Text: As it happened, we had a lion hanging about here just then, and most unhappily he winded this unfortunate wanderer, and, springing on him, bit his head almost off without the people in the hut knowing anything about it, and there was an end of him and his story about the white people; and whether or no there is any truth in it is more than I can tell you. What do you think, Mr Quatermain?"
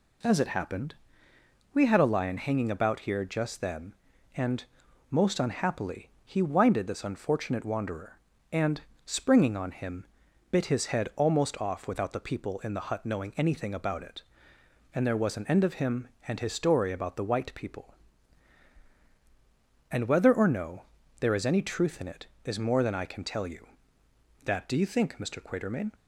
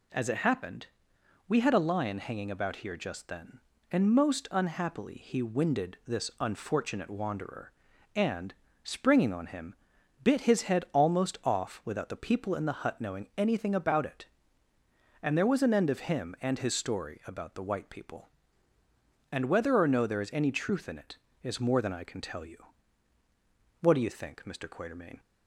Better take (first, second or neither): second